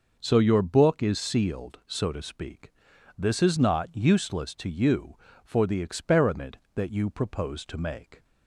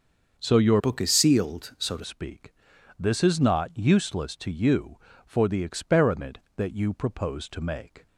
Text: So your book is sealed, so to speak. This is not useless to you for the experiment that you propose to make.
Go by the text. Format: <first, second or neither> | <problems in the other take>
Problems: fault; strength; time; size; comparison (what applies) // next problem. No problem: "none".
first | starts louder than the rest; until 1.3 s; 6.5 dB // changes voice from "book" to "to"; from 0.7 to 2.0 s; 1.3 s long